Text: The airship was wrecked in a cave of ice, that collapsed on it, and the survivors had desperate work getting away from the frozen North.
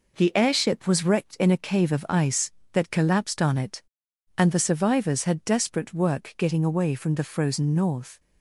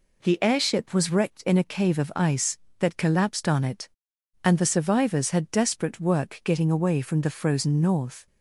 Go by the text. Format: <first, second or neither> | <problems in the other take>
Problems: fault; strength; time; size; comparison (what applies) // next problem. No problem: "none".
second | gets quieter; throughout; 4 dB